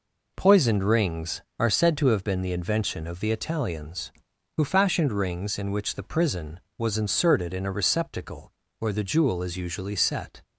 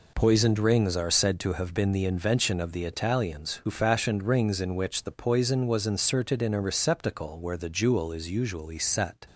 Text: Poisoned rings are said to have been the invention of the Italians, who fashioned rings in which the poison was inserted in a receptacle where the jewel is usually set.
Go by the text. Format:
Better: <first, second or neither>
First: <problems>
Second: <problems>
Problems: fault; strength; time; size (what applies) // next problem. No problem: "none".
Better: second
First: says "prison" for "poison"; at 6.0 s // pauses between "receptacle" and "where"; slight; at 8.5 s; 0.28 s long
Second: none